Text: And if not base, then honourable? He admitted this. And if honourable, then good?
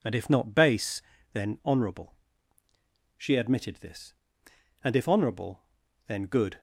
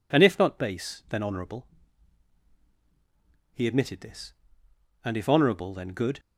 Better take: second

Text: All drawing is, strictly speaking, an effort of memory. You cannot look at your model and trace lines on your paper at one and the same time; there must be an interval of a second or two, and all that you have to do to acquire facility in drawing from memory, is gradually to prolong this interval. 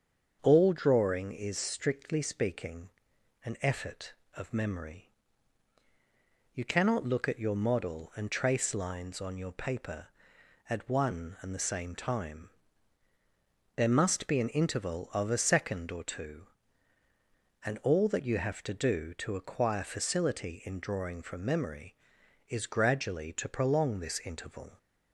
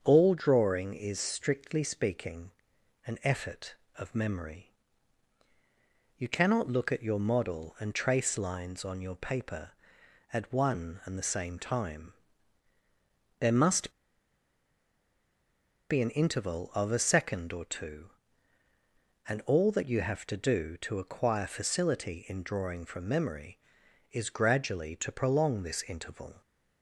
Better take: first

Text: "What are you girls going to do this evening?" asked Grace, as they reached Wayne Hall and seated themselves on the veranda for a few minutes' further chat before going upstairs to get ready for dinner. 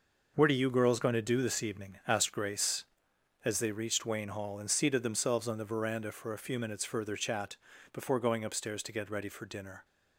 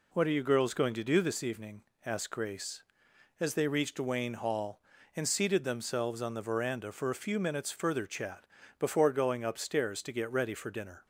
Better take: second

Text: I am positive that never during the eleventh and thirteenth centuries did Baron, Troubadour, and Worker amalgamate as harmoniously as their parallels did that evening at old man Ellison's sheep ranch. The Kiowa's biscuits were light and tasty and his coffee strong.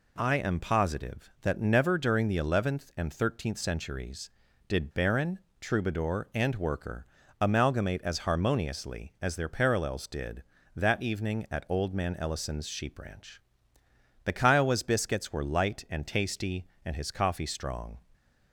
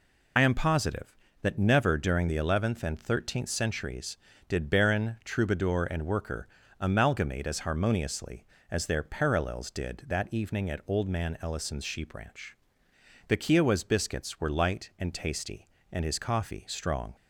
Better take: first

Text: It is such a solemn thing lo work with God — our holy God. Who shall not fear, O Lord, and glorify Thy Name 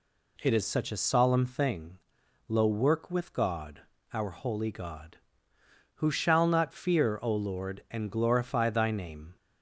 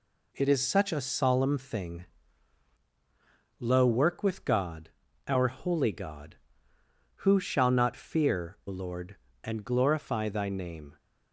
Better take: first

